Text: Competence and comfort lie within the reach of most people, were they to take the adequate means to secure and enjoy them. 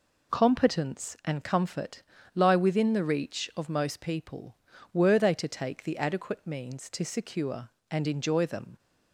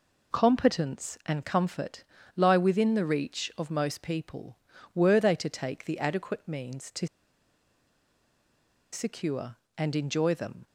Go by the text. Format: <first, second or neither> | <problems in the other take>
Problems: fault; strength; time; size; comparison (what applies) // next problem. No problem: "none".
first | pauses between "comfort" and "lie"; slight; at 2.0 s; 0.32 s long; slight in the first // pauses between "to" and "secure"; strong; at 7.0 s; 1.8 s long